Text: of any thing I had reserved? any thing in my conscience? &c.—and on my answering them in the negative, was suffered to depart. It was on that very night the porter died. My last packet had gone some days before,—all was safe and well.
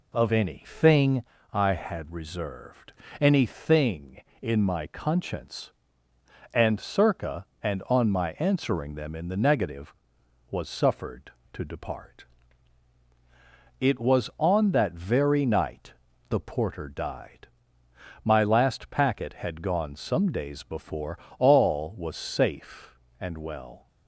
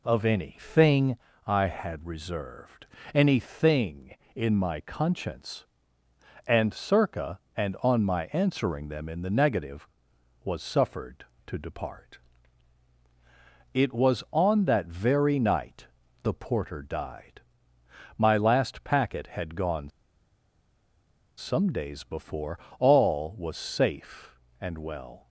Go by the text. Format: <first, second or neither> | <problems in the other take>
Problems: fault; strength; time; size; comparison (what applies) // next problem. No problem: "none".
first | pauses between "thing" and "I"; slight; at 1.1 s; 0.30 s long; slight in the first // pauses between "night" and "the"; slight; at 15.8 s; 0.36 s long; slight in the first // pauses between "gone" and "some"; strong; at 19.8 s; 1.4 s long